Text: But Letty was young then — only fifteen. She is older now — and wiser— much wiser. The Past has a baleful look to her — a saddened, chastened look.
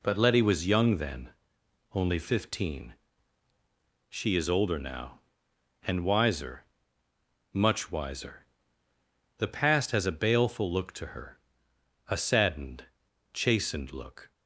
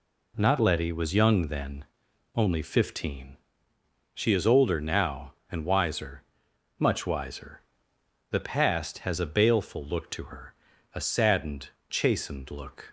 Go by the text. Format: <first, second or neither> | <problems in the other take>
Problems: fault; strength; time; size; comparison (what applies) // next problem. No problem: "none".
first | says "Not" for "But"; at 0.3 s